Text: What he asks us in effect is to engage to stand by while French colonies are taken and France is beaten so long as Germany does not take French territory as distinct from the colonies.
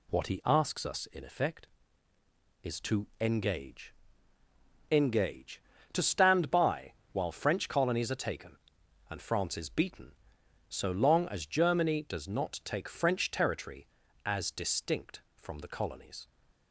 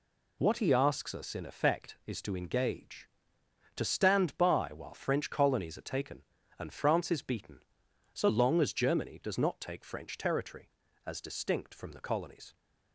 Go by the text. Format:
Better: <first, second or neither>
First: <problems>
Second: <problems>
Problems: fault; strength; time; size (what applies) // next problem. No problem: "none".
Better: second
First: says "engage" twice; at 4.9 s // pauses between "by" and "while"; slight; at 6.9 s; 0.18 s long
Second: none